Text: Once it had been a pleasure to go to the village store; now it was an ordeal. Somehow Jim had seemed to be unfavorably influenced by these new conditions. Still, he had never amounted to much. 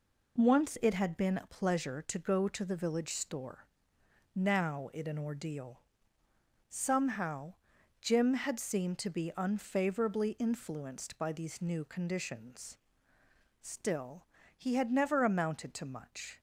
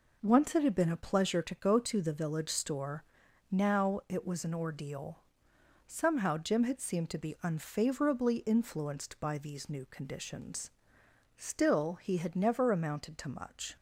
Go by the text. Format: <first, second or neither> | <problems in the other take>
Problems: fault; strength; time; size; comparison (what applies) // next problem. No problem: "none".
second | skips "was"; at 5.0 s // pauses between "Somehow" and "Jim"; noticeable; at 7.5 s; 0.48 s long